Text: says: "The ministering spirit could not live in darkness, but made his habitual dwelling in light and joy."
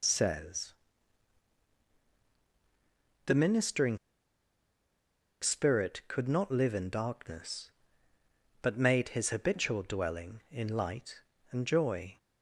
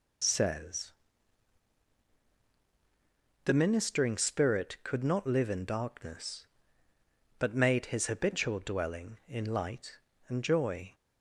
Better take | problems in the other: second | pauses between "ministering" and "spirit"; strong; at 3.9 s; 1.4 s long

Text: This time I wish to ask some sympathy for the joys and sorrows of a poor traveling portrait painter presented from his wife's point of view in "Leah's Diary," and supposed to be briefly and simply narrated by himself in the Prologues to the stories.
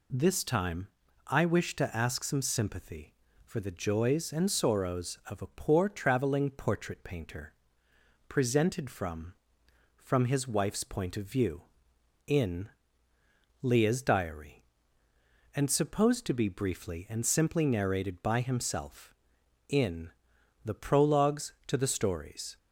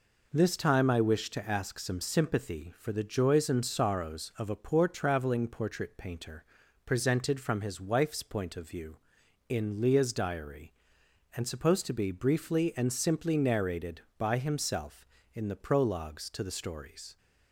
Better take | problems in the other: second | pauses between "time" and "I"; at 0.8 s; 0.38 s long // pauses between "painter" and "presented"; noticeable; at 7.5 s; 0.74 s long; also in the second // says "from" twice; at 9.9 s // pauses between "in" and "Leah's"; noticeable; at 12.6 s; 0.96 s long // pauses between "in" and "the"; noticeable; at 20.0 s; 0.56 s long

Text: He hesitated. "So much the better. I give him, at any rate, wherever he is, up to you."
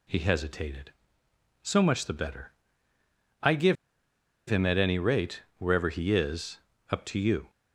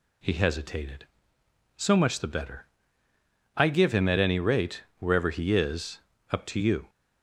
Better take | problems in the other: second | pauses between "give" and "him"; noticeable; at 3.7 s; 0.72 s long

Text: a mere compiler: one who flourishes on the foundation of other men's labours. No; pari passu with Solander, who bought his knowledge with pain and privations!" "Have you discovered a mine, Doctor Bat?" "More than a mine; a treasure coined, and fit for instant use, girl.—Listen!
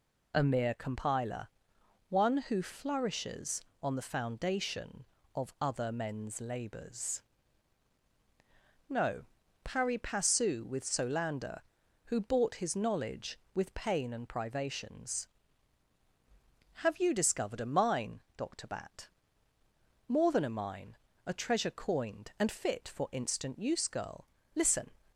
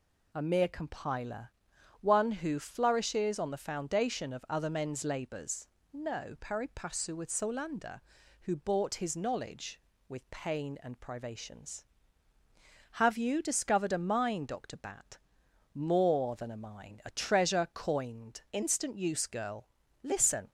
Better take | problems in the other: first | skips "and fit for"; at 18.4 s

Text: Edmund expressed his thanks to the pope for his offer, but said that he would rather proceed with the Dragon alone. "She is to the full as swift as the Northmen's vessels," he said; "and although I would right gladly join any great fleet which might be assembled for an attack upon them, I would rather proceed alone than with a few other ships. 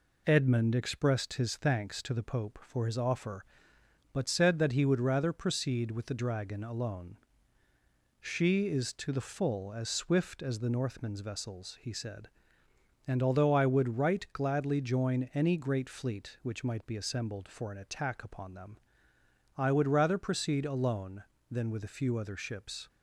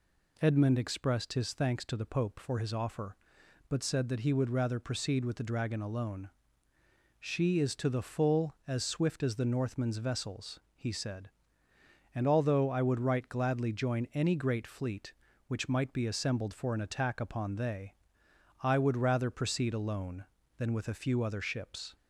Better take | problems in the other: first | says "they" for "them"; at 17.5 s

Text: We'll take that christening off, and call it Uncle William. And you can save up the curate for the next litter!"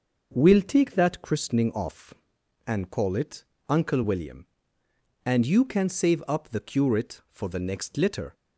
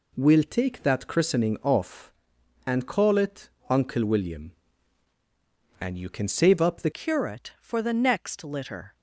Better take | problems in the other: first | pauses between "it" and "Uncle"; slight; at 3.4 s; 0.22 s long; slight in the first // changes voice at "curate"; from 6.9 s on; 2.0 s long

